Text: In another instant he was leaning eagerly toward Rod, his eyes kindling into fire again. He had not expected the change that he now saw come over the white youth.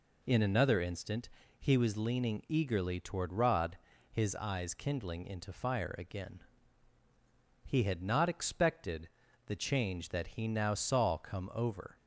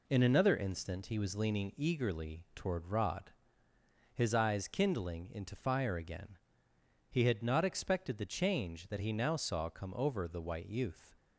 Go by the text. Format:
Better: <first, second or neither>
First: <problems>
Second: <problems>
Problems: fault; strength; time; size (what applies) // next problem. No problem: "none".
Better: second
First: pauses between "instant" and "he"; slight; at 1.2 s; 0.30 s long // pauses between "expected" and "the"; at 9.0 s; 0.38 s long // stops before "the white youth"; at 11.9 s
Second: none